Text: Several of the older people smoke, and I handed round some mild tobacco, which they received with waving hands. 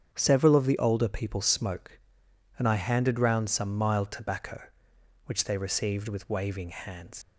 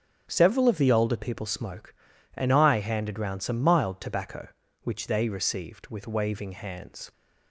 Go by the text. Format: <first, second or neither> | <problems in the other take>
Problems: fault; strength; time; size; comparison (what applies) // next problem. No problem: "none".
second | starts louder than the rest; strong; until 1.1 s; 8 dB; also in the second // leaves "hands" unfinished; at 7.2 s; 85 ms